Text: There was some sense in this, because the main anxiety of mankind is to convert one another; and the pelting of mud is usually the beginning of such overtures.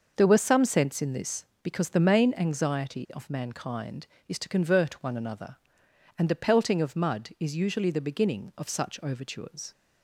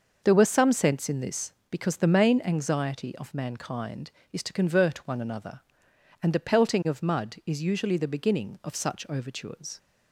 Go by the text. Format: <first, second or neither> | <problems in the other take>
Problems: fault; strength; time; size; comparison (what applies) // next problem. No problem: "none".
neither | starts louder than the rest; noticeable; the same in both